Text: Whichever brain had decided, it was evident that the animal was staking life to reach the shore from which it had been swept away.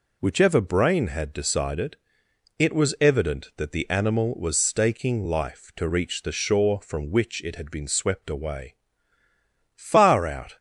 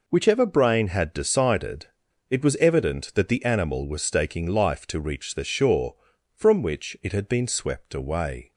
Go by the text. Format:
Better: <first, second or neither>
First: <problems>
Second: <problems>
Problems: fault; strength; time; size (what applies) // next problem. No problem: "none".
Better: second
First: goes on to say "Far out"; noticeable; from 9.7 s on; 0.82 s long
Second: none